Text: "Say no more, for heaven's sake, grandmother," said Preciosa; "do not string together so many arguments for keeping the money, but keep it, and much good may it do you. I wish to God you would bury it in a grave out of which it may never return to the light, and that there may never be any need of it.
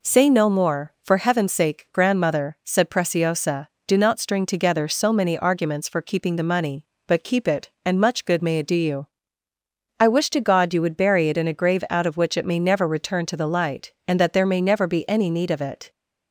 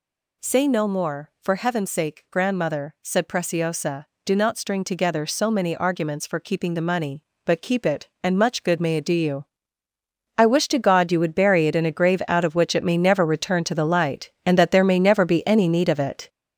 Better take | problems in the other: first | gets louder; throughout; 6.5 dB

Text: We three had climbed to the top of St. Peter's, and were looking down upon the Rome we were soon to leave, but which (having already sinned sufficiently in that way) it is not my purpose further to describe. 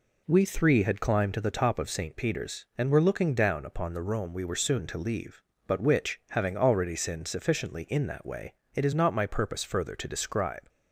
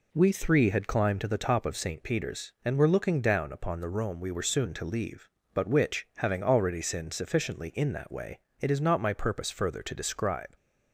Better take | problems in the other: neither | none

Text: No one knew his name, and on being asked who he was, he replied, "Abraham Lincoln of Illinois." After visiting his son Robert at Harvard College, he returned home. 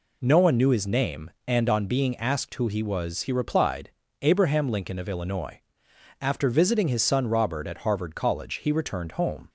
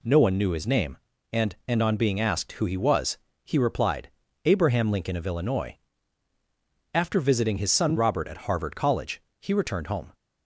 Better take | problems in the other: first | says "and" twice; at 1.6 s

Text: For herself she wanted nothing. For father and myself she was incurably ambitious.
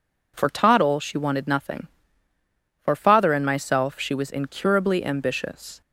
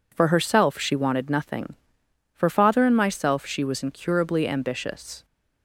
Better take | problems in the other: second | says "toddle" for "herself"; at 0.4 s

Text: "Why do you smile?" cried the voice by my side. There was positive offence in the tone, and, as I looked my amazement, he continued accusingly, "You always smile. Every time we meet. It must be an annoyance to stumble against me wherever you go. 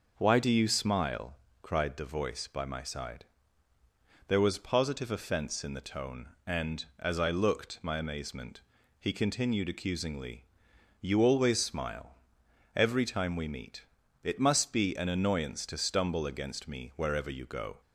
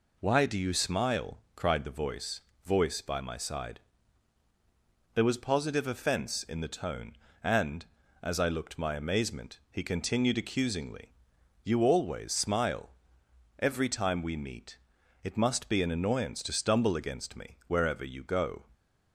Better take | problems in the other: first | says "voice" twice; at 2.6 s

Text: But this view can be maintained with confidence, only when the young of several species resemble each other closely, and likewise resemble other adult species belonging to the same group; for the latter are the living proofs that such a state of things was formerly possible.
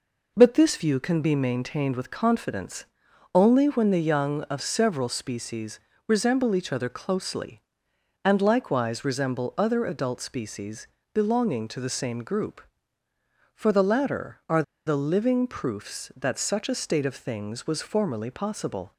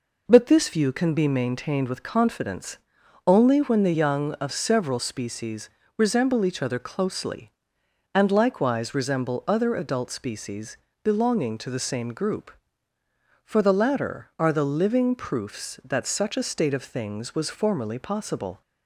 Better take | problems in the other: second | pauses between "species" and "resemble"; slight; at 5.7 s; 0.28 s long; slight in the second // pauses between "species" and "belonging"; slight; at 10.8 s; 0.26 s long; slight in the second // pauses between "are" and "the"; slight; at 14.6 s; 0.23 s long

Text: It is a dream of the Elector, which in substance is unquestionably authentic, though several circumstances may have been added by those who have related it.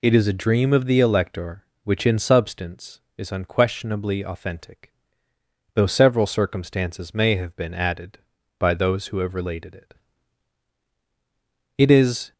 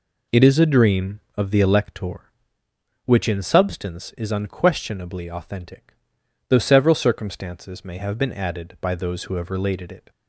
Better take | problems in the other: second | goes on to say "It is"; from 11.7 s on; 0.54 s long

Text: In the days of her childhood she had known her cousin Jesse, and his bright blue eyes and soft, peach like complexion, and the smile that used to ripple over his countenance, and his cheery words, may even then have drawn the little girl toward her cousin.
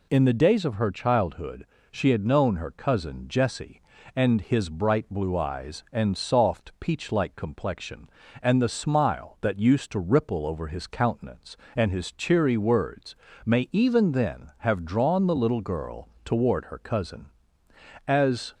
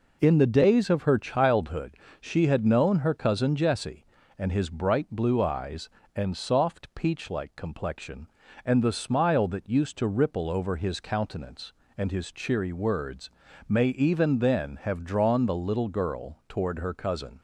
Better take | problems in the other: second | pauses between "childhood" and "she"; slight; at 1.6 s; 0.26 s long; slight in the second // pauses between "girl" and "toward"; slight; at 16.0 s; 0.16 s long // goes on to say "As"; slight; from 18.0 s on; 0.48 s long

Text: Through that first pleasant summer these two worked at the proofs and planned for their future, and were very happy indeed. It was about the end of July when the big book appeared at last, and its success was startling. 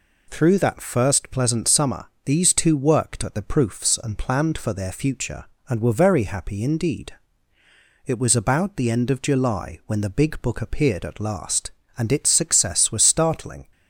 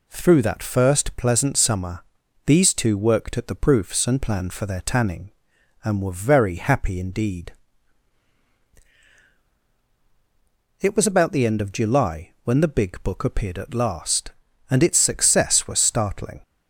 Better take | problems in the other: first | pauses between "summer" and "these"; at 2.0 s; 0.42 s long; slight in the first // says "tanning" for "future"; at 4.7 s

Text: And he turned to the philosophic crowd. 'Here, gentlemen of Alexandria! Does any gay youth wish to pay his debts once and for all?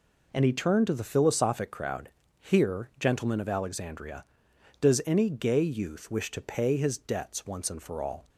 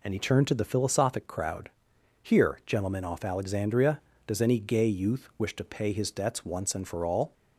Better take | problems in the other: first | says "off" for "of"; at 3.0 s

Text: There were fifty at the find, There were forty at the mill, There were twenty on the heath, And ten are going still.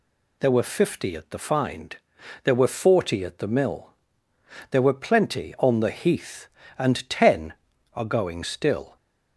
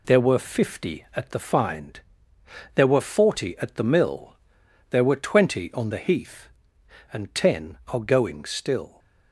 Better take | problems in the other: second | says "plenty" for "twenty"; at 4.9 s

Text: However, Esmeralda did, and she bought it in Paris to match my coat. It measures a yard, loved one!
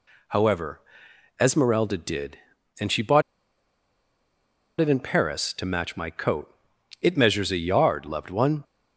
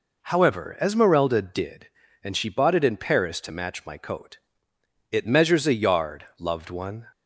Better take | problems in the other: second | pauses between "bought" and "it"; strong; at 3.2 s; 1.5 s long

